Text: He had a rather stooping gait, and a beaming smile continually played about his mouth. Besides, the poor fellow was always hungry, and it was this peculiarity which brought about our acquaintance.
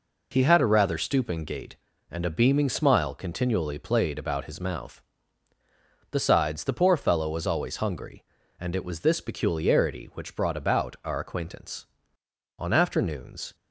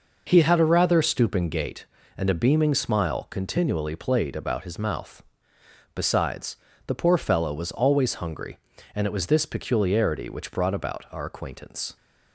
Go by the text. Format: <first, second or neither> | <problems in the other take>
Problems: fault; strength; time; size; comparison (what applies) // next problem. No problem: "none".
second | goes on to say "On afternoons"; noticeable; from 12.5 s on; 0.96 s long